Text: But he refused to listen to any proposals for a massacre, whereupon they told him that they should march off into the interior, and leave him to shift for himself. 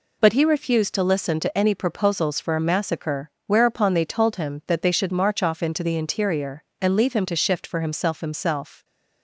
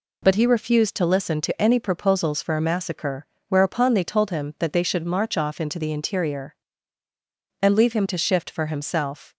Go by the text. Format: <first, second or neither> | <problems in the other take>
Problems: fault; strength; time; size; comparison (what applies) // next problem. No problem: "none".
second | says "himself" twice; at 8.2 s